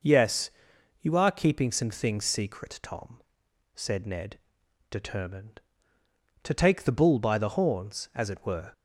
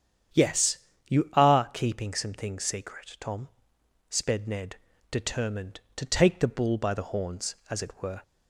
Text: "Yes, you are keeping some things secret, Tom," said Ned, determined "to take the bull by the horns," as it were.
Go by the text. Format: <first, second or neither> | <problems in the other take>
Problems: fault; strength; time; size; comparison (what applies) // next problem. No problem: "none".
first | starts louder than the rest; strong; until 1.6 s; 9 dB // says "sped" for "said"; at 4.0 s